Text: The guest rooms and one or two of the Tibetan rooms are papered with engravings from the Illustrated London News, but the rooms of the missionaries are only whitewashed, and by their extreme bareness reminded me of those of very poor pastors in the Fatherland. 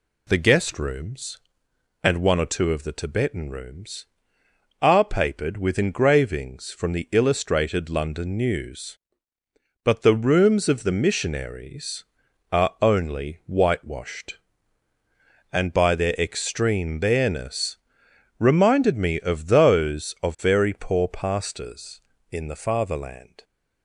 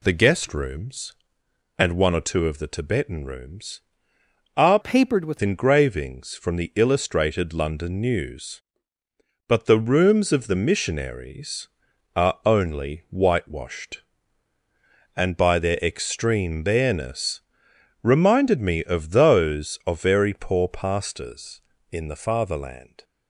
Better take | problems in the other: first | changes voice from "papered" to "with"; from 4.8 to 5.3 s; 0.5 s long // pauses between "bareness" and "reminded"; noticeable; at 17.4 s; 0.60 s long; noticeable in the first

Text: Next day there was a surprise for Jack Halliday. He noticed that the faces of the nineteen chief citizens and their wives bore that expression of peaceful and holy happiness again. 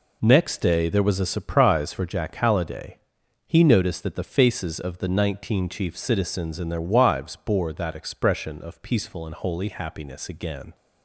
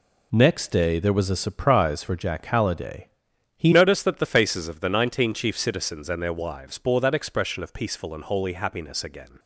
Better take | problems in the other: first | changes voice at "noticed"; from 3.7 s on; 5.6 s long

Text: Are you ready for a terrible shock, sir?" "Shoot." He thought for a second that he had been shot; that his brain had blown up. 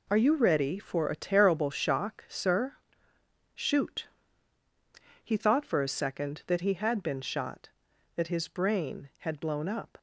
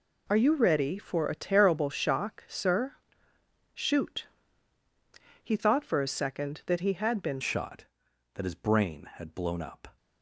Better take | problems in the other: first | changes voice at "shot"; from 7.4 s on; 2.5 s long

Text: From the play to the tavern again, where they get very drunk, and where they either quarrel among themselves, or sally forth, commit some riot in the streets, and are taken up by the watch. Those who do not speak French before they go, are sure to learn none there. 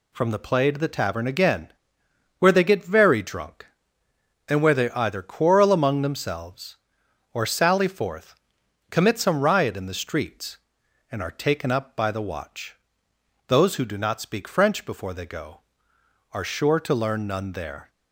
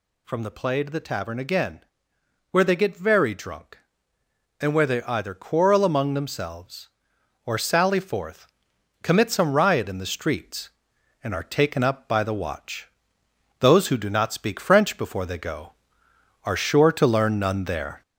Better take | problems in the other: first | gets louder; throughout; 4 dB

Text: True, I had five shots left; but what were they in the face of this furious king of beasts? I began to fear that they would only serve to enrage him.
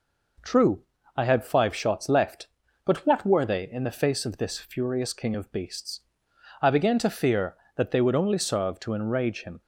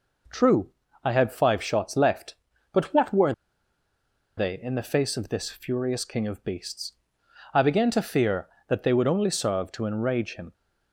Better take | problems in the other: first | pauses between "were" and "they"; at 3.3 s; 1.0 s long

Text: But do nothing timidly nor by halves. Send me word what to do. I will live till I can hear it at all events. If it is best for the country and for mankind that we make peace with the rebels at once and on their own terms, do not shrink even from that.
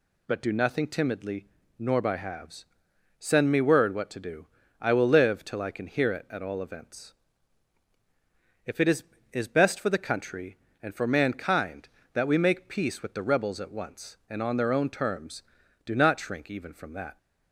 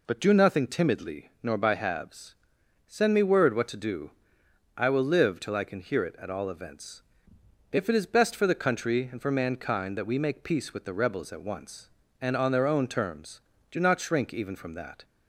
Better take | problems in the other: second | pauses between "timidly" and "nor"; slight; at 1.4 s; 0.32 s long // says "is" twice; at 9.3 s

